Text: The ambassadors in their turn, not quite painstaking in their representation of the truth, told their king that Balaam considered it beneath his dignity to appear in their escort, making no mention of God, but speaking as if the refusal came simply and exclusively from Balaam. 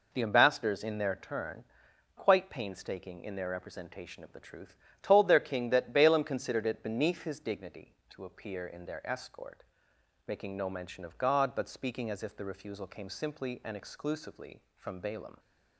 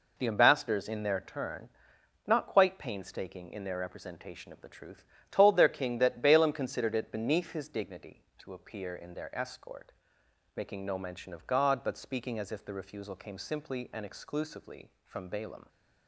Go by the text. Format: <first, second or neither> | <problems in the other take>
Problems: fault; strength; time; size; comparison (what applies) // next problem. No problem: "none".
second | skips "not"; at 1.9 s